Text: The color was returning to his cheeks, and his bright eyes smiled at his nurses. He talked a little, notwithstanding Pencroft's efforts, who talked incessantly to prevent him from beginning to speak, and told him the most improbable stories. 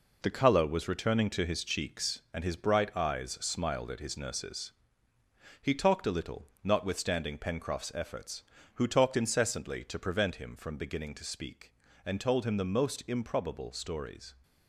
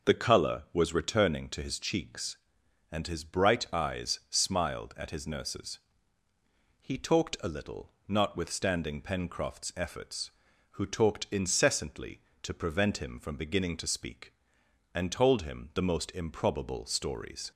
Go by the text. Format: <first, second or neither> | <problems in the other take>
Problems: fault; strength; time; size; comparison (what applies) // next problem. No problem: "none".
second | gets quieter; strong; throughout; 7 dB